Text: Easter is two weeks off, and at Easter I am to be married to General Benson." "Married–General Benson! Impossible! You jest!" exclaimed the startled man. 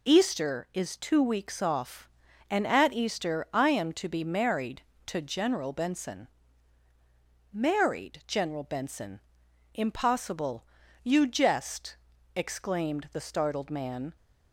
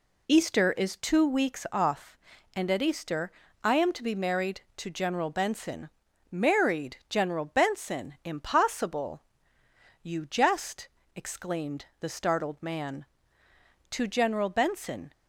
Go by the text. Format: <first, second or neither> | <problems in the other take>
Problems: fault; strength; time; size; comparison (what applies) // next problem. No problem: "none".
first | pauses between "Easter" and "I"; slight; at 3.2 s; 0.32 s long // goes on to say "To General Benson"; noticeable; from 13.8 s on; 1.2 s long